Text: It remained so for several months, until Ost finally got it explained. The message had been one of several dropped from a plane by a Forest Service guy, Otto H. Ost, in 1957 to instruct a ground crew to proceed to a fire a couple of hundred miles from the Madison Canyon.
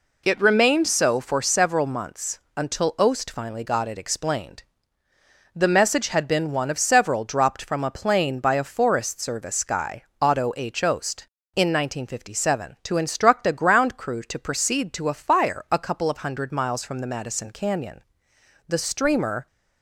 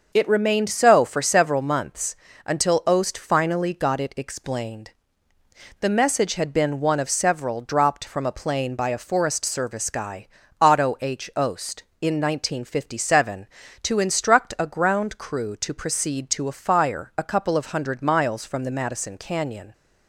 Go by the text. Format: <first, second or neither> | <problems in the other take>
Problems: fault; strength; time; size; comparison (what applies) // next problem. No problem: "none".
second | goes on to say "The streamer"; noticeable; from 18.6 s on; 0.80 s long